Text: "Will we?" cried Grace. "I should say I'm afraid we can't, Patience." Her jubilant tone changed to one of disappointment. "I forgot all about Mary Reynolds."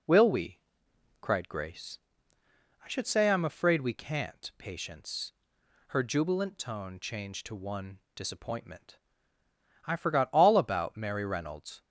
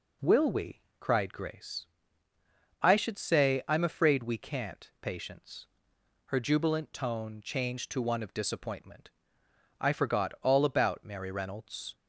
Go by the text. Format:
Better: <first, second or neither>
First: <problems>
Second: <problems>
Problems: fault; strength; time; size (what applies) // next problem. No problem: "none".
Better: second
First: skips "of"; at 8.0 s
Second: none